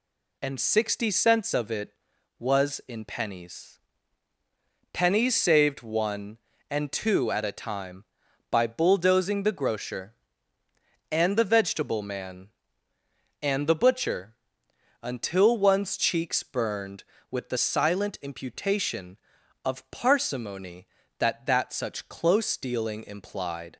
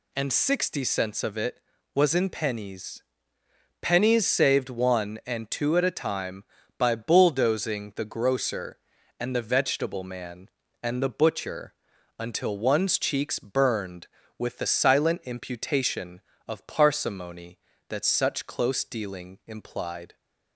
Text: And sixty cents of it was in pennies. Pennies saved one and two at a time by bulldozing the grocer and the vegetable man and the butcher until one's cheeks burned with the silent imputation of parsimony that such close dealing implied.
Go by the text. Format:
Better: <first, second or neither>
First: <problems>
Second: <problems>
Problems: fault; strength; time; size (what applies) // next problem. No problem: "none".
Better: second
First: pauses between "butcher" and "until"; noticeable; at 14.3 s; 0.68 s long // says "that" twice; at 21.4 s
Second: pauses between "butcher" and "until"; noticeable; at 11.7 s; 0.46 s long